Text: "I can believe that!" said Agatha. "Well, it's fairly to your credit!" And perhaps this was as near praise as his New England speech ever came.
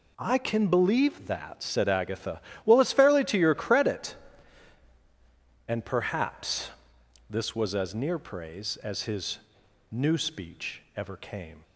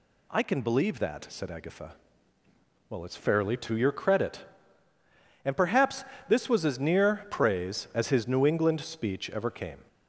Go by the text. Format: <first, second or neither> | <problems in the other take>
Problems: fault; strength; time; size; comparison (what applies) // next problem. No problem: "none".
second | pauses between "perhaps" and "this"; noticeable; at 6.6 s; 0.60 s long; slight in the second // pauses between "his" and "New"; noticeable; at 9.3 s; 0.52 s long // skips "England"; at 10.1 s